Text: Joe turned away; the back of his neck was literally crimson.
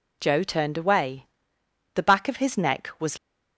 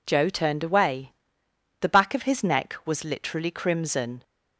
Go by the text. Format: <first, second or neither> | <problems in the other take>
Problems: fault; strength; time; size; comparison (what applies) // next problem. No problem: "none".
second | stops before "literally crimson"; at 3.1 s